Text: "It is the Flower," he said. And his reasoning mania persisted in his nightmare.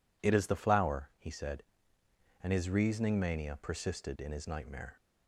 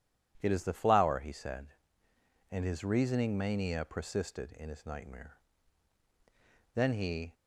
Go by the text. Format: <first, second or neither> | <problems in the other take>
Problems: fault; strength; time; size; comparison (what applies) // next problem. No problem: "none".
first | goes on to say "Then he"; from 6.7 s on; 0.60 s long